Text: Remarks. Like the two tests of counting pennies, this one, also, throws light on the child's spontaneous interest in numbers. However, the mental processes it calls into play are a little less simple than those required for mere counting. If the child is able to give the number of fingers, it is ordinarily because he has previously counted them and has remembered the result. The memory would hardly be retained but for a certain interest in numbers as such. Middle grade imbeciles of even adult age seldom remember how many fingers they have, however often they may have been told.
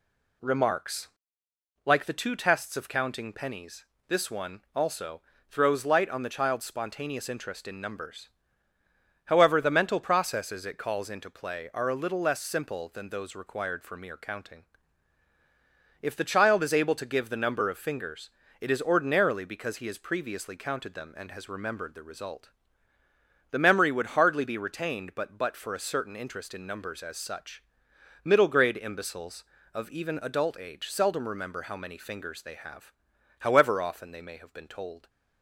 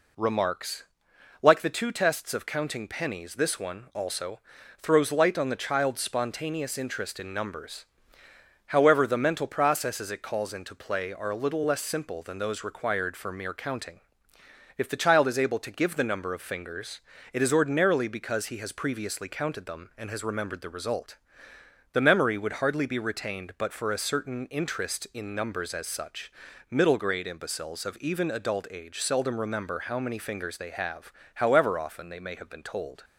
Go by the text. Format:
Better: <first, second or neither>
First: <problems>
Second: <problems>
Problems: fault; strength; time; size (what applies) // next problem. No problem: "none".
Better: second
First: says "but" twice; at 25.3 s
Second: none